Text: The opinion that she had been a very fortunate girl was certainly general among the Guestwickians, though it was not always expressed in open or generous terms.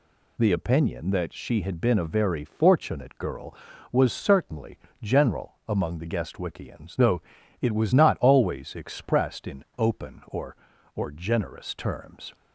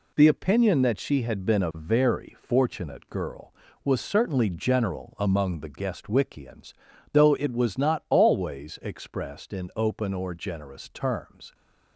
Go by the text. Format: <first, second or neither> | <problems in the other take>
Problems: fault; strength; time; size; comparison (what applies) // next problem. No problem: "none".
second | pauses between "certainly" and "general"; slight; at 4.7 s; 0.24 s long // pauses between "though" and "it"; at 7.2 s; 0.40 s long // says "or" twice; at 10.9 s